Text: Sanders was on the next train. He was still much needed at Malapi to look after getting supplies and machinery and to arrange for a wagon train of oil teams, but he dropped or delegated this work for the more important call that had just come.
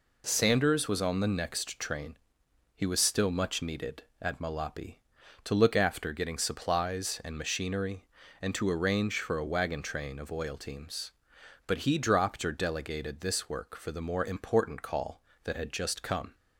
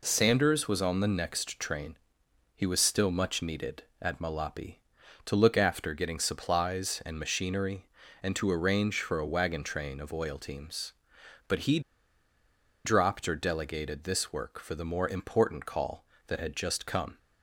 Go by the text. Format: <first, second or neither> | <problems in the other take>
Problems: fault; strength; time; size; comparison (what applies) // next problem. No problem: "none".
first | pauses between "he" and "dropped"; at 11.7 s; 1.0 s long